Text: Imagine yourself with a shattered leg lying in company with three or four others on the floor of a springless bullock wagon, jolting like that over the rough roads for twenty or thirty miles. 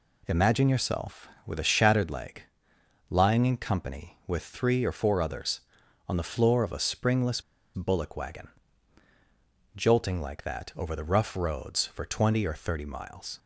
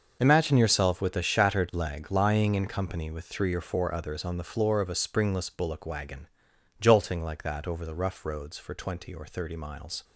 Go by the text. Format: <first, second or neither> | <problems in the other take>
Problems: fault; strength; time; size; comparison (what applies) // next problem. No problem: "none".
second | pauses between "leg" and "lying"; noticeable; at 2.4 s; 0.66 s long // pauses between "springless" and "bullock"; slight; at 7.4 s; 0.32 s long